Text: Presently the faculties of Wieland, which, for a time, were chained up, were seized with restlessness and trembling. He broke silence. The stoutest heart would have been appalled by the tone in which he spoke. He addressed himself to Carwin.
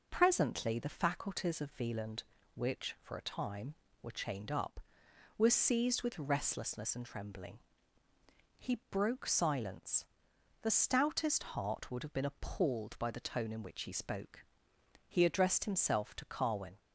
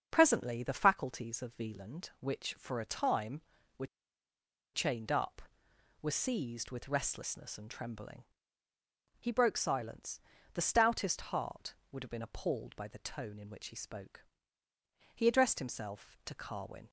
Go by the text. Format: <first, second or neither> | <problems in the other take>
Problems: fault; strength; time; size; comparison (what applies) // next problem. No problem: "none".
first | starts louder than the rest; until 1.1 s; 6.5 dB // pauses between "were" and "chained"; noticeable; at 3.8 s; 0.88 s long